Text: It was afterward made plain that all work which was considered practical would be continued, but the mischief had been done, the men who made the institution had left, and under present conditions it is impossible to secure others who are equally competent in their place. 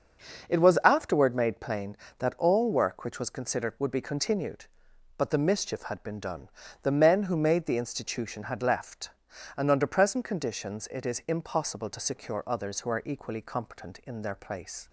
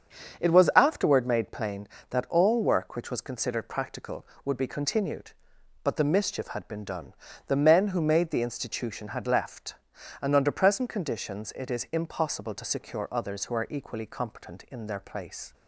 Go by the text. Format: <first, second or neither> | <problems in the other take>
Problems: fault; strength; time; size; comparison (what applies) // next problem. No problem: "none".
second | starts louder than the rest; noticeable; until 1.5 s; 6 dB; strong in the second // skips "practical"; at 3.7 s